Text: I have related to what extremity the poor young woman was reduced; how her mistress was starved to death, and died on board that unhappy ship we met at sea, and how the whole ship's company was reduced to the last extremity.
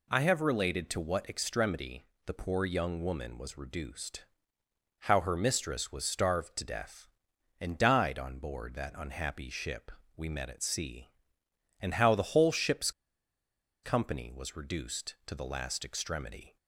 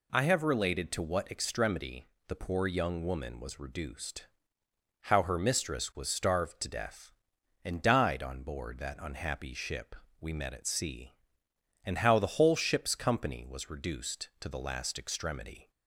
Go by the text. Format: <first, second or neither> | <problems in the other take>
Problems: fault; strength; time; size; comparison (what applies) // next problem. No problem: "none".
second | pauses between "extremity" and "the"; slight; at 2.0 s; 0.18 s long; slight in the second // pauses between "ship" and "we"; slight; at 9.9 s; 0.24 s long; slight in the second // pauses between "ship's" and "company"; noticeable; at 12.8 s; 0.93 s long